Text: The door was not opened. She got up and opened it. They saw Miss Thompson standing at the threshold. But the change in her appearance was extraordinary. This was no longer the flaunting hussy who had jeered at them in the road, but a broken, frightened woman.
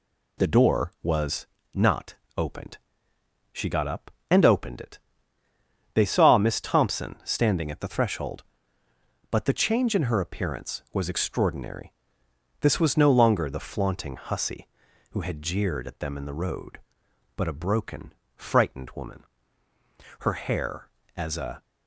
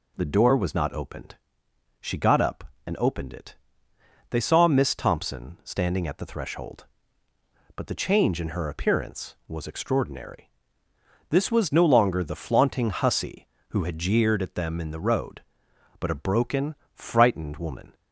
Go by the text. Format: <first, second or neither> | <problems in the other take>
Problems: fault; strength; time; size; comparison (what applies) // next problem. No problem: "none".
second | pauses between "was" and "not"; slight; at 1.4 s; 0.28 s long // pauses between "not" and "opened"; slight; at 2.1 s; 0.22 s long // goes on to say "Her hair as a"; from 20.1 s on; 1.4 s long